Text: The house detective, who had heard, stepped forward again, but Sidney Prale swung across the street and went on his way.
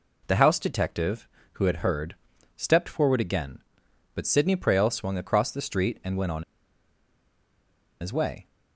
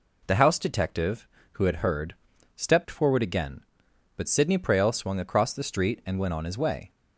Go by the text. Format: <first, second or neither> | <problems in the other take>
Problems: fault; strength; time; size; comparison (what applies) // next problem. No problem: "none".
second | pauses between "on" and "his"; strong; at 6.4 s; 1.5 s long